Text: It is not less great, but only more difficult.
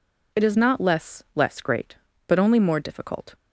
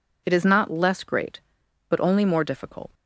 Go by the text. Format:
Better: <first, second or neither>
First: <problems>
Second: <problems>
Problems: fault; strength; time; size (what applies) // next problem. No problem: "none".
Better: second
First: says "less" twice; at 1.3 s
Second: none